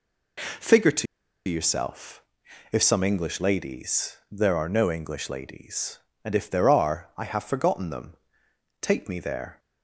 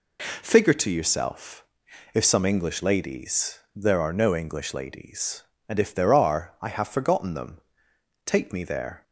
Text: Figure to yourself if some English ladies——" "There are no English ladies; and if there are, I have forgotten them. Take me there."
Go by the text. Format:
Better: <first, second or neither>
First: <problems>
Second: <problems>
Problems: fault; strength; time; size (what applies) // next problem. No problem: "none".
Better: second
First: pauses between "to" and "yourself"; at 1.0 s; 0.43 s long // pauses between "yourself" and "if"; noticeable; at 2.2 s; 0.48 s long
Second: pauses between "yourself" and "if"; noticeable; at 1.6 s; 0.48 s long